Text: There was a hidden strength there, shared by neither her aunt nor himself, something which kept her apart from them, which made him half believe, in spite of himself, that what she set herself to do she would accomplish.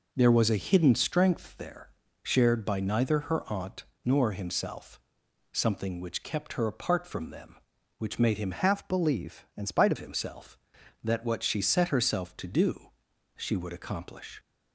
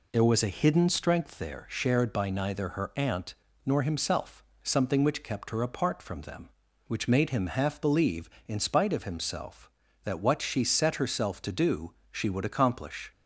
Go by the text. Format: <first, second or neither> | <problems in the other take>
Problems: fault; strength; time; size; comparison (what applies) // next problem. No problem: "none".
second | pauses between "aunt" and "nor"; slight; at 3.8 s; 0.18 s long; slight in the second // changes voice from "half" to "of"; from 8.5 to 9.9 s; 1.4 s long // pauses between "do" and "she"; noticeable; at 12.8 s; 0.50 s long; slight in the second